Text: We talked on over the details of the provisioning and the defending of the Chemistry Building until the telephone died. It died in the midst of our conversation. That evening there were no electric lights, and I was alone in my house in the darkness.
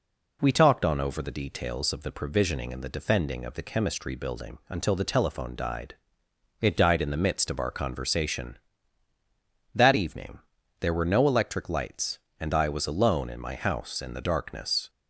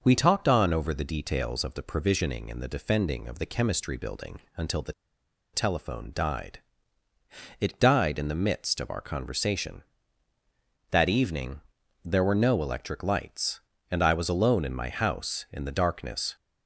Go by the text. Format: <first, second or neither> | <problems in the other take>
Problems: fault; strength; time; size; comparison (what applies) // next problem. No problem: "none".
first | starts louder than the rest; noticeable; until 1.0 s; 6 dB // pauses between "Building" and "until"; slight; at 4.3 s; 0.16 s long // pauses between "the" and "telephone"; noticeable; at 4.9 s; 0.61 s long // pauses between "evening" and "there"; at 11.6 s; 0.42 s long; also in the first